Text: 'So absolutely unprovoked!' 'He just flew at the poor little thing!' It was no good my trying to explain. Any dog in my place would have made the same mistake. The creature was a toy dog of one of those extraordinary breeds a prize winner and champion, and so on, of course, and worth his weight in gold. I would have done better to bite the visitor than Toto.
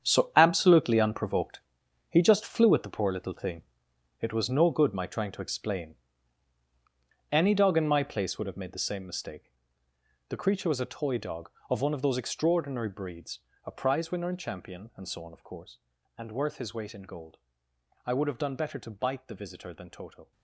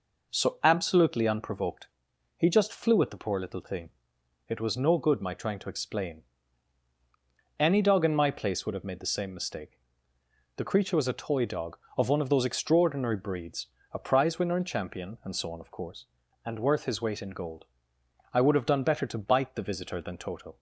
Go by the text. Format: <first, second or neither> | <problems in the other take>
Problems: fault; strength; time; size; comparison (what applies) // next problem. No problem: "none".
second | gets quieter; strong; throughout; 12 dB // pauses between "breeds" and "a"; slight; at 13.3 s; 0.24 s long; slight in the second